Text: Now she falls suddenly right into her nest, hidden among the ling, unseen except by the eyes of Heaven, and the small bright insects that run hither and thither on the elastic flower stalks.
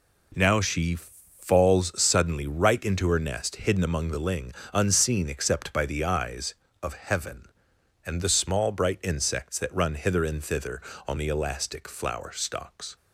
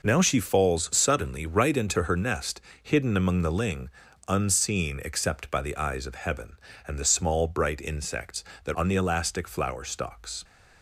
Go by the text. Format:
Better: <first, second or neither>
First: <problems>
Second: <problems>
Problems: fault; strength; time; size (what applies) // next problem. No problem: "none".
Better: first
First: none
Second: skips "run hither and thither"; at 8.7 s